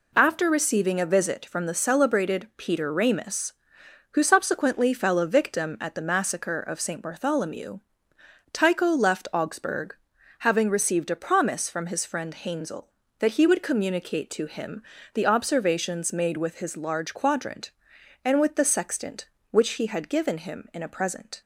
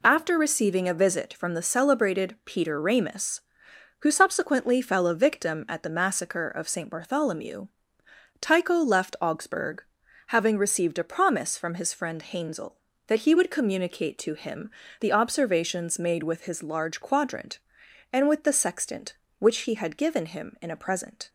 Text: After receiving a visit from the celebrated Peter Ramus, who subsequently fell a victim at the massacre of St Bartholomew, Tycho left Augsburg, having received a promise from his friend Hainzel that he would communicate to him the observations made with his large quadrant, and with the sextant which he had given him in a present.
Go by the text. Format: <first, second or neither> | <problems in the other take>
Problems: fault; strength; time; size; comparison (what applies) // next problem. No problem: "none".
neither | pauses between "him" and "the"; slight; the same in both